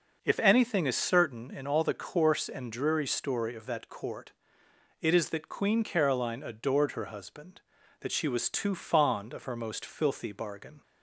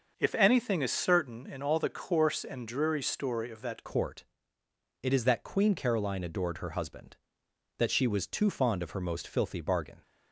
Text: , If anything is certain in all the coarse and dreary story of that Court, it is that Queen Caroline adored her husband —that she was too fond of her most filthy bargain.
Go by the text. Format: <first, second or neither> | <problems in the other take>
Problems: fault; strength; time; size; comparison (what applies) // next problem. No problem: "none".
first | starts louder than the rest; until 1.1 s; 6 dB // changes voice at "Court"; from 3.8 s on; 6.2 s long